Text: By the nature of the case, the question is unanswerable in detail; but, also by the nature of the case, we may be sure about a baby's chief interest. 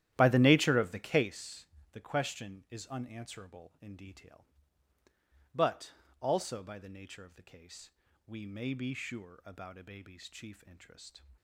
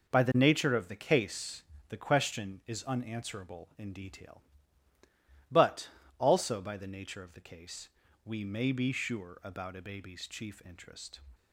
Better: second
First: starts louder than the rest; strong; until 1.4 s; 12 dB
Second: none

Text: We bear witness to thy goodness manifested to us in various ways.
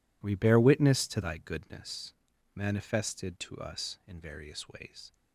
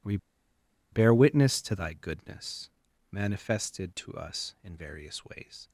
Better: first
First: pauses between "goodness" and "manifested"; at 2.1 s; 0.40 s long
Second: pauses between "We" and "bear"; noticeable; at 0.1 s; 0.75 s long // pauses between "goodness" and "manifested"; at 2.6 s; 0.40 s long

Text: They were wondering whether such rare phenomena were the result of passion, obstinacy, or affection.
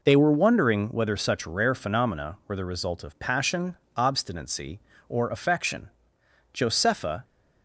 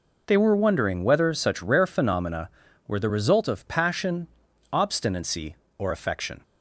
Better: second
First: goes on to say "Josepha"; noticeable; from 6.5 s on; 0.70 s long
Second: none

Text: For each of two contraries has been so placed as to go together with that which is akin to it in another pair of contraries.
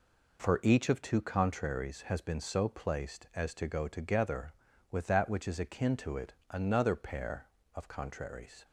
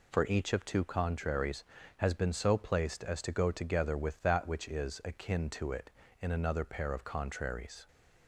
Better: second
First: skips "in"; at 6.4 s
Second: none

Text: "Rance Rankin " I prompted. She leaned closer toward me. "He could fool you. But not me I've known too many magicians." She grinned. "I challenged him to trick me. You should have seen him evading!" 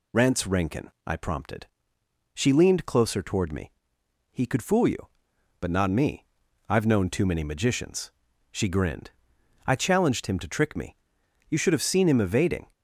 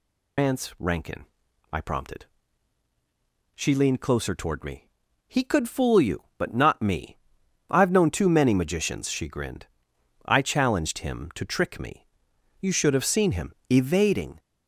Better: first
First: pauses between "me" and "I've"; at 6.2 s; 0.42 s long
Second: loses the start of "Rance"; at 0.3 s; 160 ms // pauses between "me" and "I've"; noticeable; at 7.1 s; 0.52 s long // pauses between "him" and "evading"; slight; at 13.5 s; 0.16 s long

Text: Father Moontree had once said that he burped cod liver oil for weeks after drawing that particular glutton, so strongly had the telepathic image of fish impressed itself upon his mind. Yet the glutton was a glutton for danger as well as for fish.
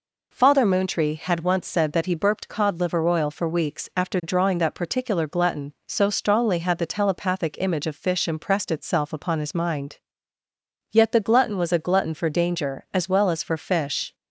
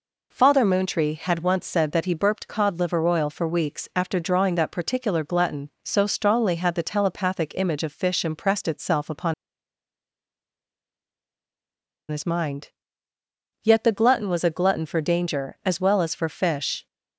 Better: first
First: none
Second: pauses between "upon" and "his"; strong; at 9.3 s; 2.7 s long

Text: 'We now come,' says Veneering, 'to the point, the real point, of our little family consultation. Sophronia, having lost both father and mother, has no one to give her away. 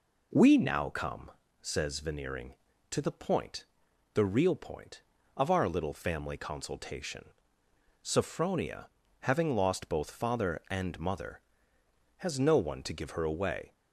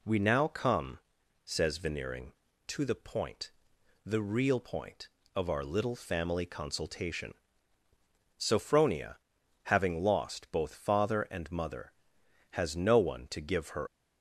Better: first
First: none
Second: stops before "away"; at 13.8 s

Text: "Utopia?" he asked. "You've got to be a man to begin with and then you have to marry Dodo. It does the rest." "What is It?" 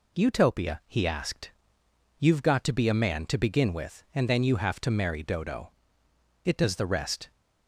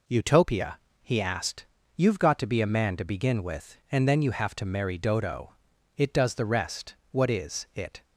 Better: second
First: stops before "What is It"; at 7.3 s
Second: none

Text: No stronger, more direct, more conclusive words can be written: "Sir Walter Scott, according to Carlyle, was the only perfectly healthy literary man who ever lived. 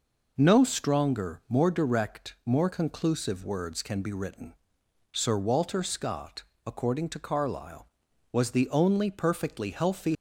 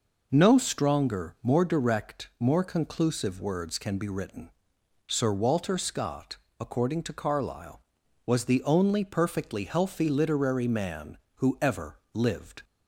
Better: second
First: stops before "literary man who ever lived"; at 10.1 s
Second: none

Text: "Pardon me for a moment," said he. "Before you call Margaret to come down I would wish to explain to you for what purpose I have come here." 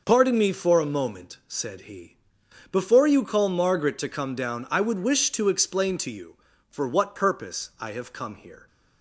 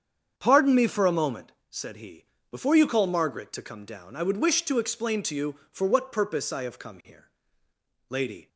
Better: first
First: none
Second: starts louder than the rest; strong; until 1.3 s; 7.5 dB // goes on to say "Lady"; slight; from 8.0 s on; 0.40 s long

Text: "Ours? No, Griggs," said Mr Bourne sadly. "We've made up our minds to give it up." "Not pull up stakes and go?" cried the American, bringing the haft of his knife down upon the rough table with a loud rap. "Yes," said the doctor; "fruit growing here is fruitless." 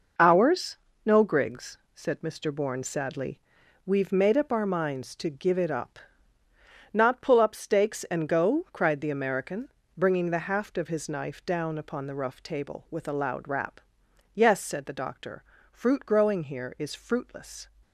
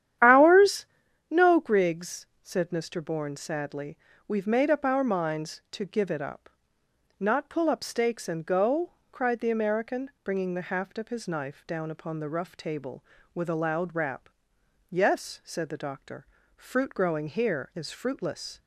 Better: first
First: none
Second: starts louder than the rest; strong; until 1.2 s; 10.5 dB

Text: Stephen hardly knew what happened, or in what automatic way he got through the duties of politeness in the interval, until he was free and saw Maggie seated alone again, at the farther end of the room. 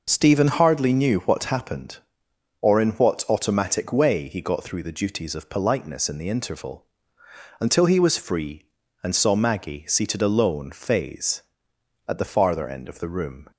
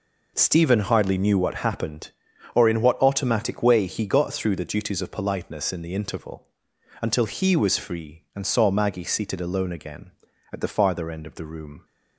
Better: second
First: says "phase" for "again"; at 10.7 s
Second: none

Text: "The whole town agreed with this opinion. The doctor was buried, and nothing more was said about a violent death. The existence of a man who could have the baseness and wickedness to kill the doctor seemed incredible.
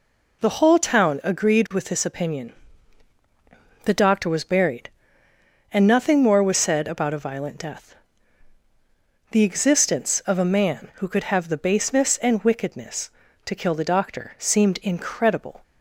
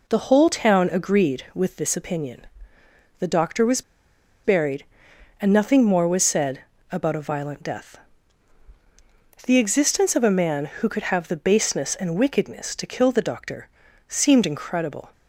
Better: first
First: none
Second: pauses between "was" and "buried"; noticeable; at 3.8 s; 0.63 s long // pauses between "said" and "about"; slight; at 6.5 s; 0.32 s long // pauses between "doctor" and "seemed"; at 13.6 s; 0.40 s long

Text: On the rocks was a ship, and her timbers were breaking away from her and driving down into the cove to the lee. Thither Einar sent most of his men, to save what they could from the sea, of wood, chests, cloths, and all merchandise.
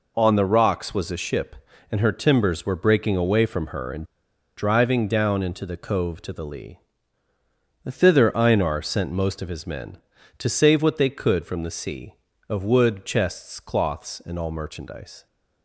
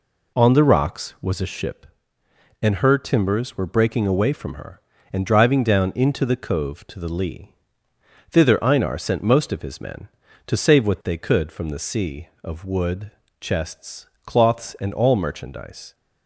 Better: second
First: pauses between "and" and "driving"; noticeable; at 4.0 s; 0.51 s long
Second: none

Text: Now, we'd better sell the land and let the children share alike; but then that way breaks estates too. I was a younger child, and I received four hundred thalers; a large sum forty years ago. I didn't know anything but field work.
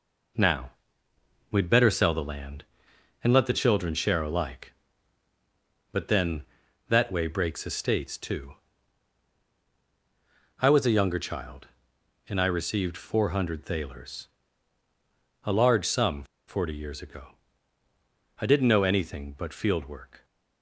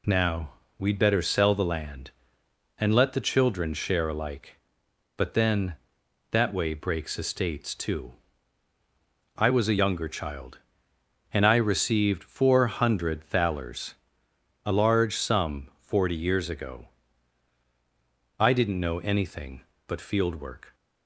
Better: second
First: pauses between "sum" and "forty"; slight; at 16.2 s; 0.23 s long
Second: none

